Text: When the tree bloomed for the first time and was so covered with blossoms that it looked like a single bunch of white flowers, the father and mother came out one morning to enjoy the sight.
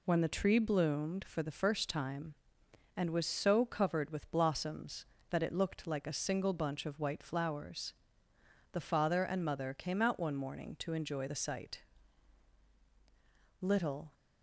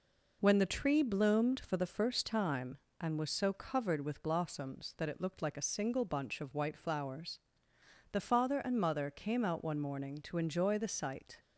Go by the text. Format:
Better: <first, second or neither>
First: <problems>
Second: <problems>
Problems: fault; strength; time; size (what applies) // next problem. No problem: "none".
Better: second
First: goes on to say "Little"; from 13.6 s on; 0.52 s long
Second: none